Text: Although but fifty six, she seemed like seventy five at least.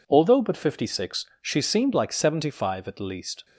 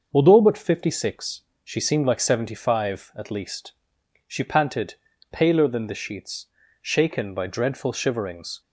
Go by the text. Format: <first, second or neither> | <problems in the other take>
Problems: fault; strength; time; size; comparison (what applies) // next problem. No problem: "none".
first | starts louder than the rest; until 1.1 s; 6.5 dB // goes on to say "She panted paler than the sheets shaken by dreadful shiverings"; strong; from 4.2 s on; 4.3 s long